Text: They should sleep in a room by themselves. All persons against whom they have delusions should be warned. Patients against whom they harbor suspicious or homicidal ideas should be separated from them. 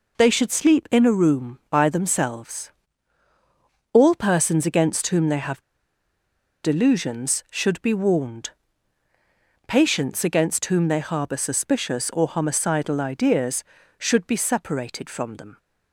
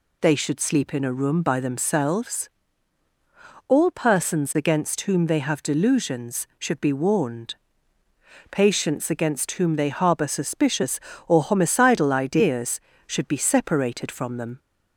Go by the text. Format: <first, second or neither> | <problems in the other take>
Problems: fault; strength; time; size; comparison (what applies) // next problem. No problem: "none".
second | pauses between "have" and "delusions"; at 5.6 s; 1.0 s long